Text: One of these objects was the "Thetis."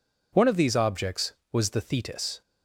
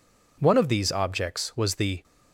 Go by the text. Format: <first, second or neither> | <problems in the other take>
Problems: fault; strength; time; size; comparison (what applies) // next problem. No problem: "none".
first | stops before "Thetis"; at 2.0 s